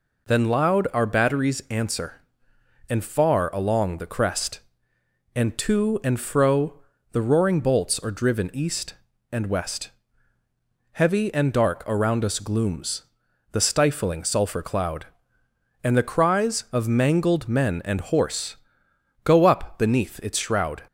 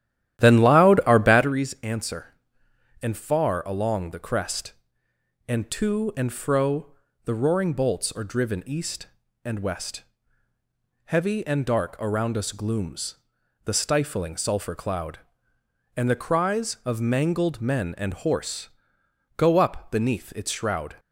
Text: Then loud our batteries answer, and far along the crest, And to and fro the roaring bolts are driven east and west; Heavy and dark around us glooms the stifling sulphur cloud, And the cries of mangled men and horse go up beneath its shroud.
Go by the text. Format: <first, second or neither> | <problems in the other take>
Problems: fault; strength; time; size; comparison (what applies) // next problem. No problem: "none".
first | starts louder than the rest; strong; until 1.6 s; 12.5 dB // pauses between "fro" and "the"; slight; at 6.9 s; 0.30 s long; slight in the first // pauses between "glooms" and "the"; noticeable; at 13.1 s; 0.50 s long; noticeable in the first // pauses between "horse" and "go"; noticeable; at 18.6 s; 0.68 s long; noticeable in the first